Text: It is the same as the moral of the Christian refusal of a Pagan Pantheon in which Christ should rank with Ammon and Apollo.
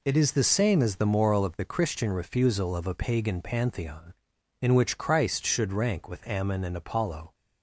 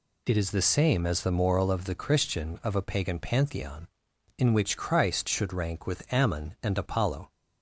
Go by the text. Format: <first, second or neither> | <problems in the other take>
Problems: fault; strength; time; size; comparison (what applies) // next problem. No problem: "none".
first | skips "refusal"; at 2.6 s